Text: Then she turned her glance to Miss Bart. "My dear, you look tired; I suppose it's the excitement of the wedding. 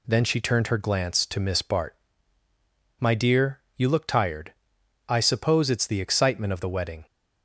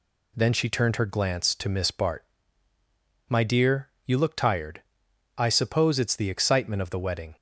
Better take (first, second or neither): neither